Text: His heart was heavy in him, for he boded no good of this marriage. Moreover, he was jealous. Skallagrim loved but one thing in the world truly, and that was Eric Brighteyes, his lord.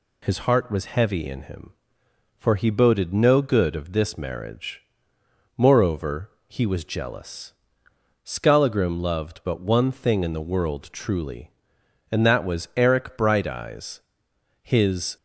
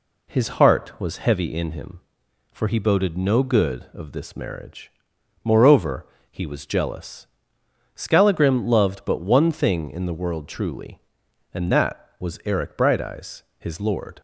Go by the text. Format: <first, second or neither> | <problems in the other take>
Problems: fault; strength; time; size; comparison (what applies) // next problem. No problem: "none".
second | stops before "lord"; at 15.1 s